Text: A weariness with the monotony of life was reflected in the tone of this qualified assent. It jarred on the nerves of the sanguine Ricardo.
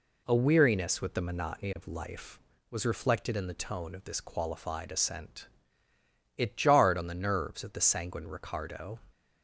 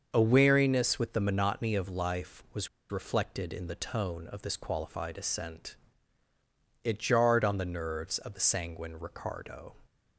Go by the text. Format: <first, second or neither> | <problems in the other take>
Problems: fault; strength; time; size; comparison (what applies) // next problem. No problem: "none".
first | starts louder than the rest; until 1.1 s; 6.5 dB // pauses between "was" and "reflected"; slight; at 2.6 s; 0.22 s long